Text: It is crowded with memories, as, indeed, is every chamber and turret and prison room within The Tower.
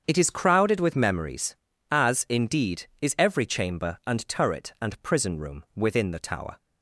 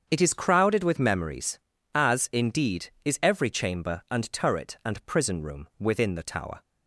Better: neither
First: starts louder than the rest; strong; until 1.0 s; 7.5 dB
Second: starts louder than the rest; strong; until 1.1 s; 7.5 dB

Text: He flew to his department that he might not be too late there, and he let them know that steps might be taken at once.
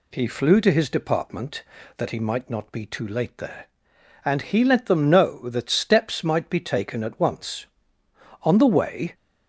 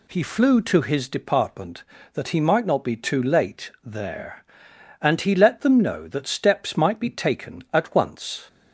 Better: second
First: goes on to say "On the way"; noticeable; from 8.4 s on; 0.72 s long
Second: none

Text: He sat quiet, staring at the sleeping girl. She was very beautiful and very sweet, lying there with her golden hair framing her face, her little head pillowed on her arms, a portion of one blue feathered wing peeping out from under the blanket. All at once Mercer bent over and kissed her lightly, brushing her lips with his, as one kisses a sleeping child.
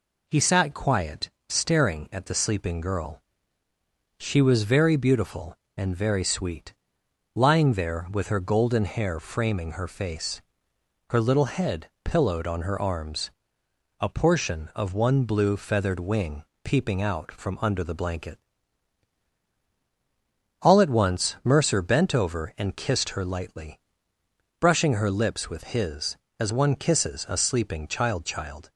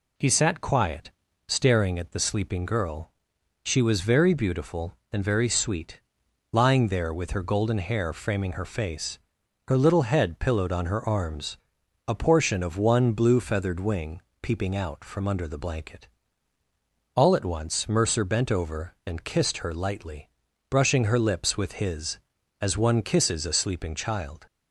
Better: second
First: pauses between "head" and "pillowed"; slight; at 11.8 s; 0.16 s long // pauses between "wing" and "peeping"; slight; at 16.4 s; 0.22 s long // says "child" twice; at 28.2 s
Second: pauses between "wing" and "peeping"; slight; at 14.2 s; 0.20 s long

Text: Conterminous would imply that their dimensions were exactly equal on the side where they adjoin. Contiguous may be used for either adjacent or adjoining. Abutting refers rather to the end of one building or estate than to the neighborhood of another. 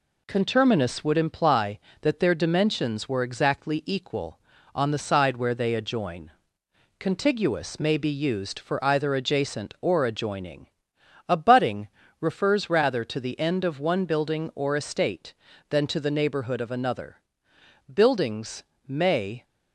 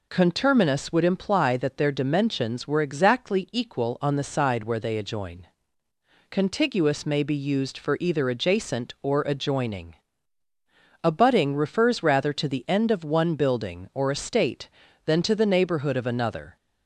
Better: second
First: pauses between "Abutting" and "refers"; slight; at 11.8 s; 0.32 s long // goes on to say "Buildings may"; from 17.9 s on; 1.5 s long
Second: none

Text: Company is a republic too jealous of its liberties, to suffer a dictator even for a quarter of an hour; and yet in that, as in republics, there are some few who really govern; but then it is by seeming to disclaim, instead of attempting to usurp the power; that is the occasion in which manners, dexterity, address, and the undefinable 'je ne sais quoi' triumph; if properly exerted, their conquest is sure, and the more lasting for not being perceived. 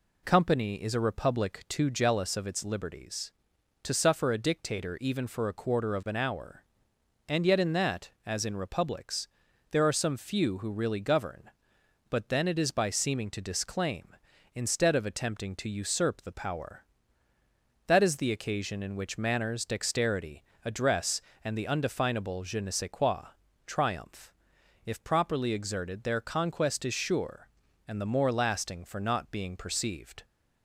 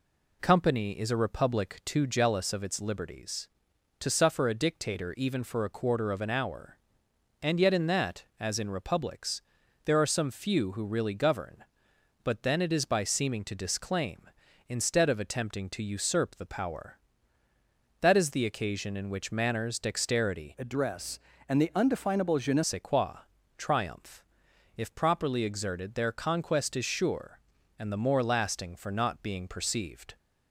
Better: first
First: pauses between "quoi" and "triumph"; slight; at 23.2 s; 0.36 s long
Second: changes voice from "address" to "ne"; from 20.5 to 22.6 s; 2.1 s long // pauses between "quoi" and "triumph"; slight; at 23.1 s; 0.36 s long

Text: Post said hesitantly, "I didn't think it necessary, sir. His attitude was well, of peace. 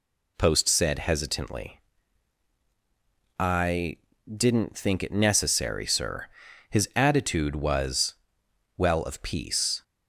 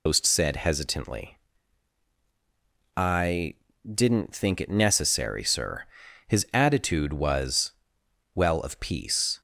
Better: first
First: pauses between "I" and "didn't"; slight; at 3.9 s; 0.32 s long // pauses between "was" and "well"; noticeable; at 8.1 s; 0.62 s long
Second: loses the start of "Post"; at 0.0 s; 115 ms // pauses between "I" and "didn't"; slight; at 3.5 s; 0.32 s long // pauses between "was" and "well"; noticeable; at 7.7 s; 0.62 s long

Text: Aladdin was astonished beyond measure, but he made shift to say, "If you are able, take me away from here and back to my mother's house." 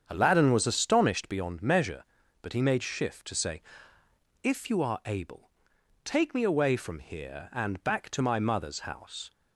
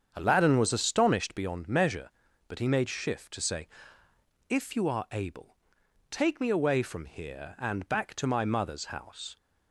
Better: neither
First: starts louder than the rest; strong; until 1.0 s; 7.5 dB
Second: starts louder than the rest; strong; until 1.1 s; 7.5 dB

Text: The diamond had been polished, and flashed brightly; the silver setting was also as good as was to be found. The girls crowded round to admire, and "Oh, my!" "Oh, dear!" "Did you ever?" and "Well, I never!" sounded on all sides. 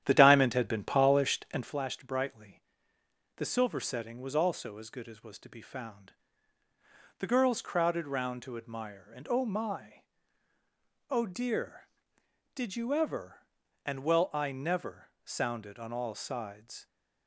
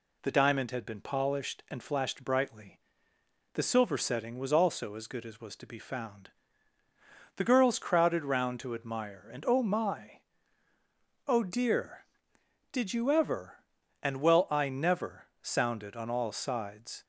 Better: second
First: starts louder than the rest; strong; until 1.8 s; 10.5 dB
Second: none

